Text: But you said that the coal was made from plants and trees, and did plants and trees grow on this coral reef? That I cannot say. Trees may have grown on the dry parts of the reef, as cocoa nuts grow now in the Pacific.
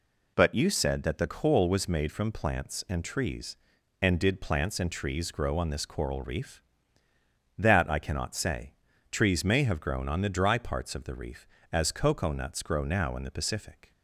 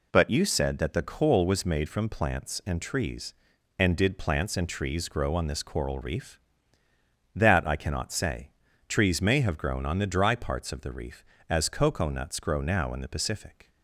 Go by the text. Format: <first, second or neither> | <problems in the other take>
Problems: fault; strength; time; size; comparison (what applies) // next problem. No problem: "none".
neither | none